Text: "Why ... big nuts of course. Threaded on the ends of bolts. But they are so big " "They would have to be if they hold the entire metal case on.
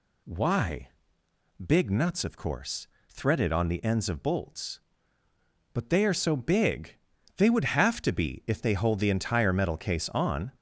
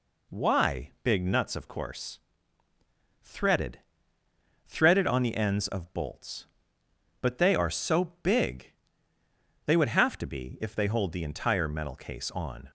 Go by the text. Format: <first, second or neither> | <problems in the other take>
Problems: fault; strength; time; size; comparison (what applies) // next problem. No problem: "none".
first | says "Threaded" twice; at 4.6 s